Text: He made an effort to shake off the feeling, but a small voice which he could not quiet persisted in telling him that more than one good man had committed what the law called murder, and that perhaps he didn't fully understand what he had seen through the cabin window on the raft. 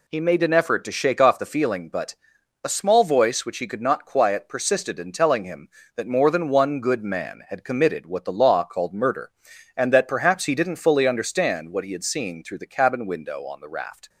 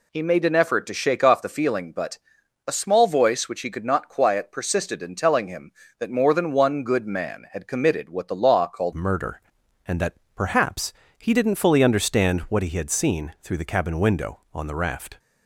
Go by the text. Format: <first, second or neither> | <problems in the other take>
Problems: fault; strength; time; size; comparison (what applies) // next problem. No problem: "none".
first | pauses between "but" and "a"; noticeable; at 2.1 s; 0.48 s long; noticeable in the first // changes voice at "murder"; from 8.9 s on; 6.2 s long // pauses between "that" and "perhaps"; slight; at 10.1 s; 0.20 s long // pauses between "perhaps" and "he"; slight; at 10.9 s; 0.24 s long